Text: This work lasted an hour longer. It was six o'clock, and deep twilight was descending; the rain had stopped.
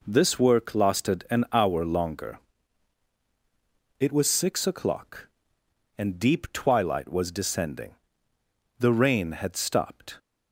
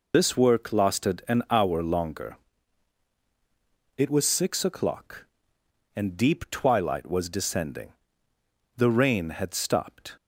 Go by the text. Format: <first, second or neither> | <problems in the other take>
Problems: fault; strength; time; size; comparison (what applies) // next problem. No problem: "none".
first | loses the start of "This"; at 0.1 s; 155 ms